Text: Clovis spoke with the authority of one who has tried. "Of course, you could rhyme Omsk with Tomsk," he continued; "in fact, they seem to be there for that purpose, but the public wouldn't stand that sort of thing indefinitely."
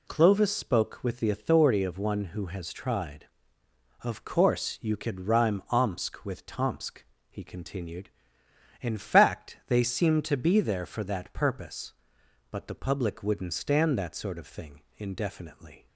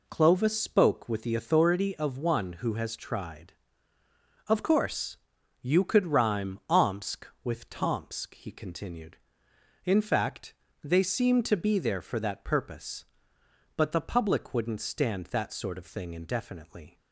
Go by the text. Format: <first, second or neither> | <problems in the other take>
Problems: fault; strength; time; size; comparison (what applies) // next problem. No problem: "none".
neither | none